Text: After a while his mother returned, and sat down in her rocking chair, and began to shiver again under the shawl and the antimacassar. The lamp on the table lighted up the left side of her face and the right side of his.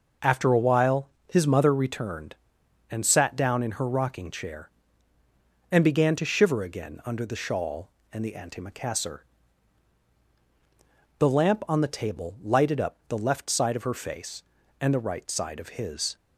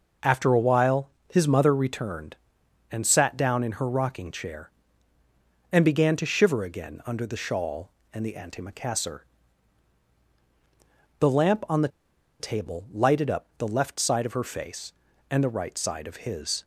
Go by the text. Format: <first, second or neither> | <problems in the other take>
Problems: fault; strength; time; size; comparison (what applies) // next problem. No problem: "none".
first | pauses between "while" and "his"; slight; at 1.1 s; 0.20 s long; slight in the first // pauses between "the" and "table"; noticeable; at 11.8 s; 0.51 s long